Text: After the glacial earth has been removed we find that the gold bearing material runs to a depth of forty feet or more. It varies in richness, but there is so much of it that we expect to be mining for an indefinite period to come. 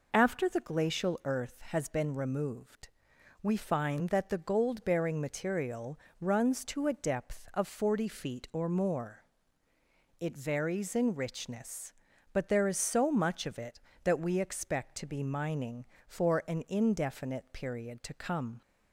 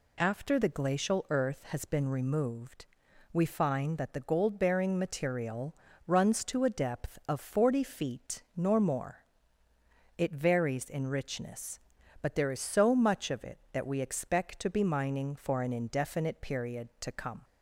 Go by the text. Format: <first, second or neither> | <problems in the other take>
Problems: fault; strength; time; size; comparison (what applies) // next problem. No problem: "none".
first | pauses between "removed" and "we"; at 2.8 s; 0.44 s long; noticeable in the first // pauses between "material" and "runs"; slight; at 5.7 s; 0.30 s long; slight in the first // says "nor" for "or"; at 8.5 s